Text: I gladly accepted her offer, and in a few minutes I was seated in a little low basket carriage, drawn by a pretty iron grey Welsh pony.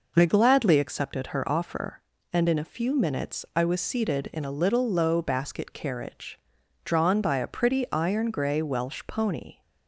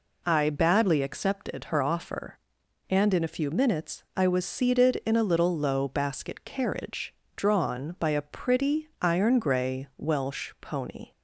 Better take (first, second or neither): first